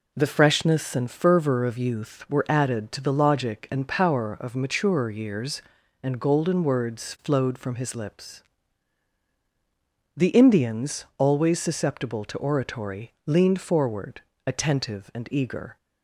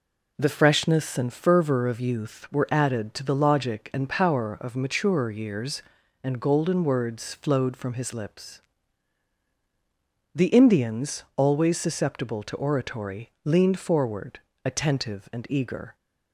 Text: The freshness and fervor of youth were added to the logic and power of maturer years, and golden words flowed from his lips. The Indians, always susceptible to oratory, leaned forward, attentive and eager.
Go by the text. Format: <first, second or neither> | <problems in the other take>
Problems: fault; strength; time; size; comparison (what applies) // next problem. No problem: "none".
neither | none